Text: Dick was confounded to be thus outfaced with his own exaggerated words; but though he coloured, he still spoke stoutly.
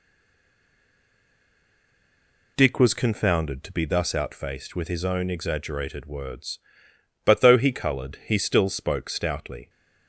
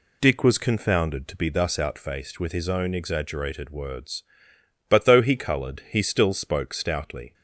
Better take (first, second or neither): second